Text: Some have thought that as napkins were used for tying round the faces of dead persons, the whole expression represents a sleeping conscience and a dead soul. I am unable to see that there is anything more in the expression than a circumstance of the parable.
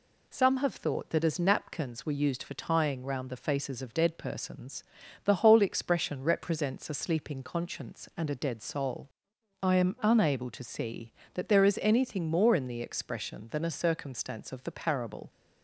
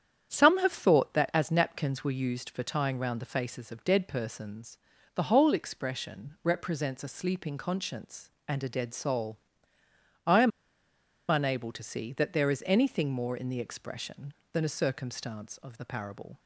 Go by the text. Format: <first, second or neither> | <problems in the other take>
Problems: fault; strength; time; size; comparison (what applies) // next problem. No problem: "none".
first | starts louder than the rest; strong; until 1.3 s; 9 dB // pauses between "am" and "unable"; noticeable; at 10.5 s; 0.80 s long